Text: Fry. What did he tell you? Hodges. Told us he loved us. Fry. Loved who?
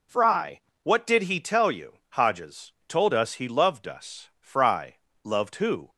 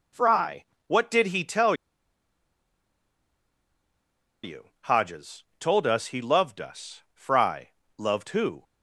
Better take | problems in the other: first | pauses between "tell" and "you"; strong; at 1.7 s; 2.6 s long

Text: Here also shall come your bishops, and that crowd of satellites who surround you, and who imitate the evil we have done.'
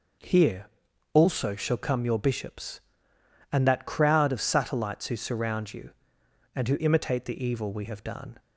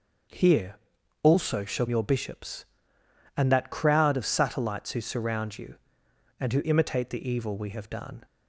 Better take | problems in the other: first | starts louder than the rest; until 1.7 s; 6 dB // pauses between "Here" and "also"; noticeable; at 0.7 s; 0.46 s long; noticeable in the first // skips "come"; at 1.8 s

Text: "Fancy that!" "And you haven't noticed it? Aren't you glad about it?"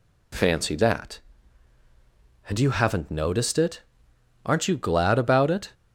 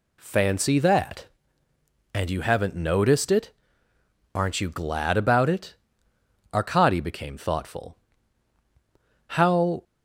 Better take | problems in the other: first | goes on to say "Arkady became thoughtful How"; strong; from 6.5 s on; 3.3 s long

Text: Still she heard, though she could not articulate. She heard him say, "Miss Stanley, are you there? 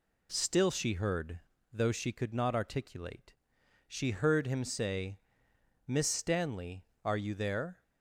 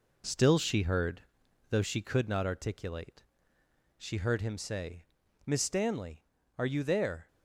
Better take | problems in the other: first | gets quieter; noticeable; throughout; 5 dB

